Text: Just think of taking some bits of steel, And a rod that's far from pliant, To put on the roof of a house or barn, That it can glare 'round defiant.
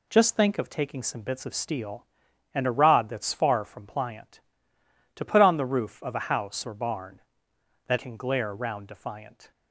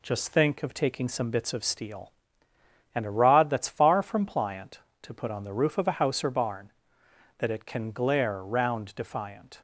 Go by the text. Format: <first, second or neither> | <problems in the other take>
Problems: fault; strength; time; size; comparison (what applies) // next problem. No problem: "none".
second | skips "it"; at 7.9 s